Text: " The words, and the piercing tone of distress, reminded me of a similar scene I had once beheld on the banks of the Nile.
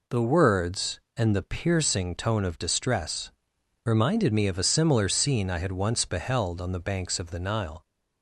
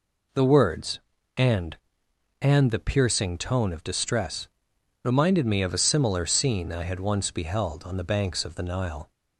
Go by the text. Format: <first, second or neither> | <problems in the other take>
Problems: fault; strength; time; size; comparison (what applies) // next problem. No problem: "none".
first | says "and" twice; at 2.4 s